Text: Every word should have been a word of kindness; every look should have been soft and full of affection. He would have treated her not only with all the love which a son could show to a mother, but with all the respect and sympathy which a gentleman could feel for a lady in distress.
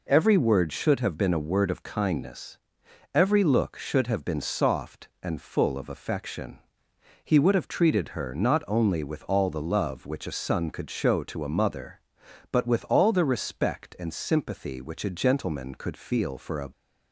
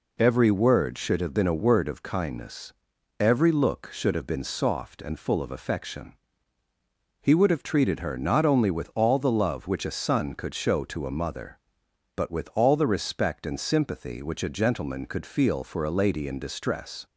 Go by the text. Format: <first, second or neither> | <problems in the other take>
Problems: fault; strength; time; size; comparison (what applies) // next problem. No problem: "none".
second | stops before "lady in distress"; at 16.7 s